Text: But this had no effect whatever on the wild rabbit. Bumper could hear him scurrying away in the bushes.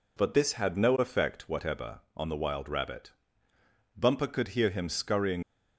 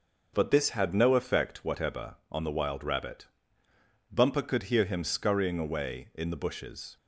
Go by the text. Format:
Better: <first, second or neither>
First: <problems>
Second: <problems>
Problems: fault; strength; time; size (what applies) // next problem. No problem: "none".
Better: second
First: stops before "away in the bushes"; at 5.4 s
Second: none